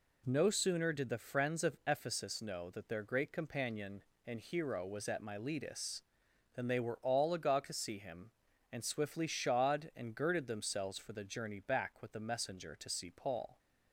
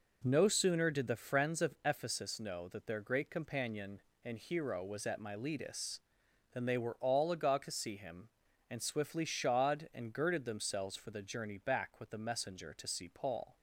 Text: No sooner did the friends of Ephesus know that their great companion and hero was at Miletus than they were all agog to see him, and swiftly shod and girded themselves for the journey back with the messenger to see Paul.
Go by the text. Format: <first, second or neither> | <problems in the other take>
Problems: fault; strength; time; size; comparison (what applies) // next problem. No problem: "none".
first | starts louder than the rest; noticeable; until 1.5 s; 4 dB